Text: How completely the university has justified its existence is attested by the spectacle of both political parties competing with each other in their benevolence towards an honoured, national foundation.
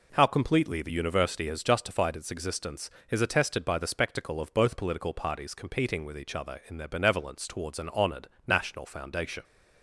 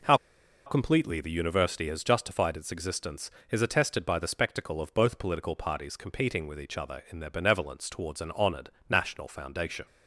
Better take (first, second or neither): first